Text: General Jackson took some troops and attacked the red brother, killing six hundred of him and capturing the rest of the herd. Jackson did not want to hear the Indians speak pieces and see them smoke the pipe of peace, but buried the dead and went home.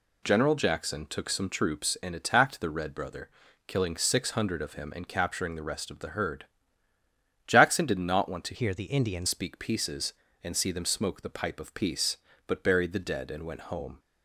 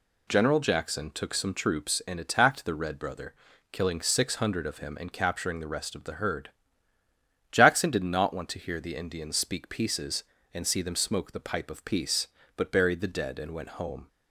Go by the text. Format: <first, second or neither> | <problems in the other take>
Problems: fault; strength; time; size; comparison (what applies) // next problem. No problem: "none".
second | changes voice from "hear" to "Indians"; from 8.5 to 9.2 s; 0.7 s long